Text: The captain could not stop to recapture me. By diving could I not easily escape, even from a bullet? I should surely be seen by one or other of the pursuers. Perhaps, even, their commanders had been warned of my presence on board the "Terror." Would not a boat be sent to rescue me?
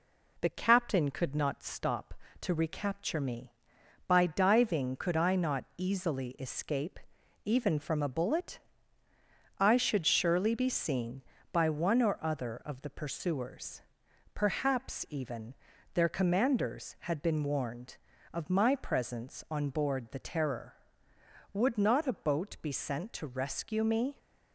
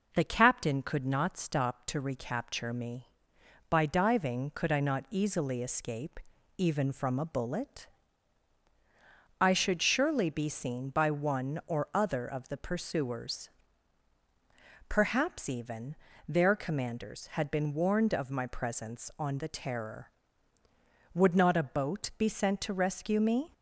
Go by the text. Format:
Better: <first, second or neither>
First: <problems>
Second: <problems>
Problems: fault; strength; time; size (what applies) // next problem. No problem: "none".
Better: first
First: none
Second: skips "board"; at 19.3 s